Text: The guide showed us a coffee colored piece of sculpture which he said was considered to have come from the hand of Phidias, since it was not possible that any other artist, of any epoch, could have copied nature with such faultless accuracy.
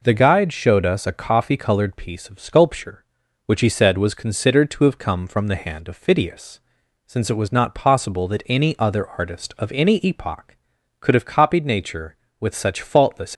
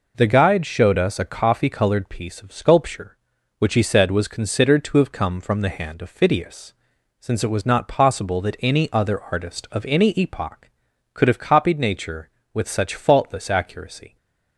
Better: second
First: stops before "accuracy"; at 13.3 s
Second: none

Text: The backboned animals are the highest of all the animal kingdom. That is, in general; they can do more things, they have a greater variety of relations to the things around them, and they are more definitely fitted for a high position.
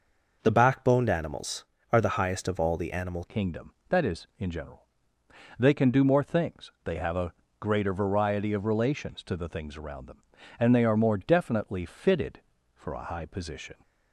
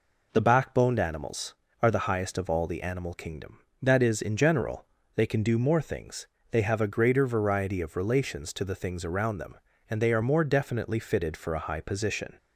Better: second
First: changes voice at "kingdom"; from 3.2 s on; 10.5 s long // pauses between "a" and "greater"; slight; at 7.3 s; 0.26 s long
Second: none

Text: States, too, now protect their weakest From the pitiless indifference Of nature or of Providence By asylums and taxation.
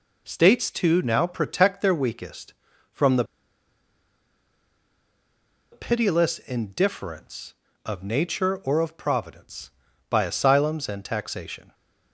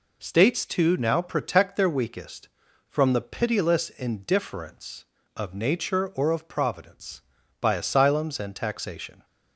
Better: second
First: pauses between "the" and "pitiless"; strong; at 3.2 s; 2.4 s long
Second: none

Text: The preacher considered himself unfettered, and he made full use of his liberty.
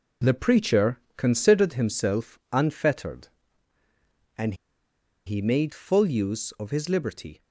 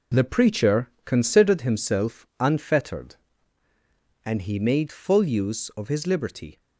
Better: second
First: pauses between "preacher" and "considered"; slight; at 0.9 s; 0.18 s long // pauses between "and" and "he"; noticeable; at 4.5 s; 0.72 s long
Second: pauses between "preacher" and "considered"; slight; at 0.8 s; 0.16 s long

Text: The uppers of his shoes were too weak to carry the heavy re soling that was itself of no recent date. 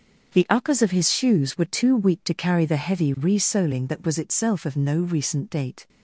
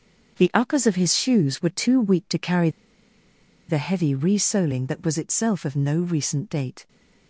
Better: first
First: starts louder than the rest; until 1.3 s; 7 dB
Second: starts louder than the rest; until 1.3 s; 7 dB // pauses between "carry" and "the"; at 2.6 s; 0.99 s long

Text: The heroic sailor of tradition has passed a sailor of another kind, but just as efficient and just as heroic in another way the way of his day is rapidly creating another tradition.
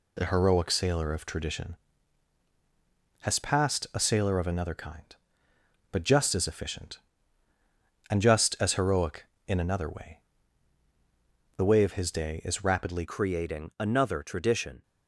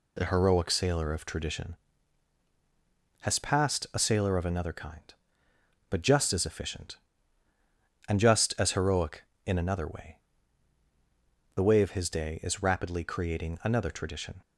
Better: second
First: pauses between "way" and "the"; strong; at 10.1 s; 1.3 s long // changes voice at "creating"; from 13.0 s on; 1.8 s long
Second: pauses between "way" and "the"; strong; at 10.1 s; 1.3 s long

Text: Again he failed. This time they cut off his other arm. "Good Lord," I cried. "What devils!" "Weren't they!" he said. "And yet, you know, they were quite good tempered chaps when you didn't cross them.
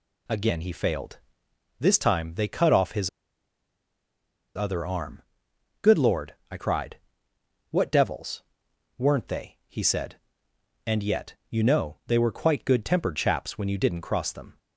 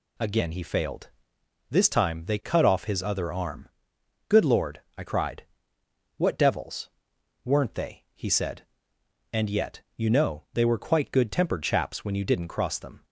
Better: second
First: pauses between "his" and "other"; strong; at 3.0 s; 1.4 s long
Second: none

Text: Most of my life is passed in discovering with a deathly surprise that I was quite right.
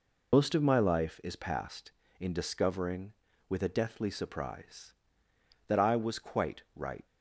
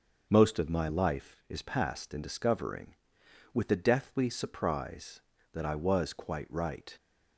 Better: second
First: loses the start of "Most"; at 0.3 s; 105 ms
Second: none

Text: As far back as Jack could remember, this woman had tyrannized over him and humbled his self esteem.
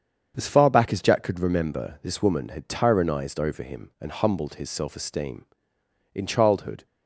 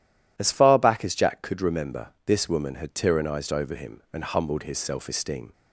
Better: second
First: starts louder than the rest; strong; until 1.3 s; 7.5 dB // goes on to say "In childhood"; noticeable; from 6.1 s on; 0.72 s long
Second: none

